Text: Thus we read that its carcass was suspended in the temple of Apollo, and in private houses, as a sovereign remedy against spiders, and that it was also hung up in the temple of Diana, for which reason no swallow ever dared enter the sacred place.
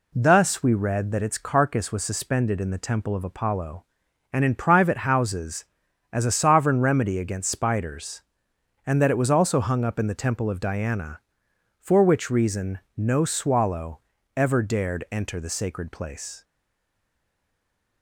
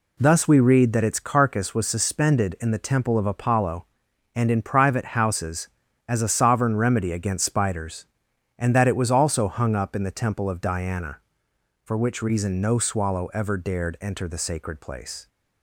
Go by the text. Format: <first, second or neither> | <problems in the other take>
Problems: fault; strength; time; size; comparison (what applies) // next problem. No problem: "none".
second | pauses between "reason" and "no"; slight; at 12.7 s; 0.18 s long // pauses between "swallow" and "ever"; slight; at 13.9 s; 0.36 s long // stays silent after the last word; noticeable; from 16.4 s on; 1.6 s long